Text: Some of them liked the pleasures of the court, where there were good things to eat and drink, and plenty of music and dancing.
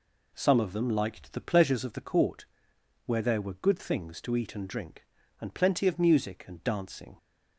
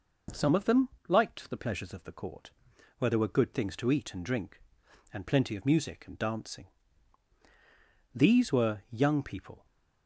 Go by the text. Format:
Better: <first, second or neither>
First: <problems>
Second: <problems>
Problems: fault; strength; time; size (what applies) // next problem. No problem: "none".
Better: first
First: none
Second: pauses between "them" and "liked"; slight; at 0.8 s; 0.18 s long // goes on to say "These were young people"; from 8.1 s on; 1.4 s long